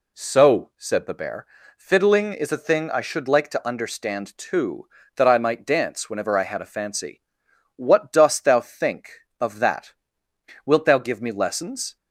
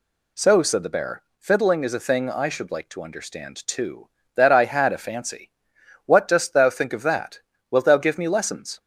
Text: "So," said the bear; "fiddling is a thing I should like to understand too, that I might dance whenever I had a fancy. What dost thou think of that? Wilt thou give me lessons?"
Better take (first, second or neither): first